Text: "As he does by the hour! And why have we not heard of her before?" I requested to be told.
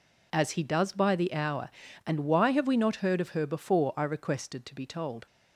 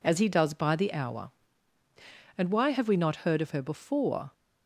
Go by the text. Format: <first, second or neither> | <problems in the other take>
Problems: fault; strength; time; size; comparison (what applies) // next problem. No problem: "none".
first | stops before "I requested to be told"; at 4.3 s